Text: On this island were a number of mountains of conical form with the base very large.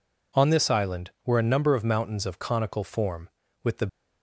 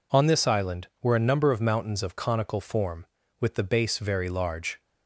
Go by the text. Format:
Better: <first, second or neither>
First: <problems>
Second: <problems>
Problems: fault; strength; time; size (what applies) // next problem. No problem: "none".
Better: second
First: stops before "base very large"; at 3.8 s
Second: none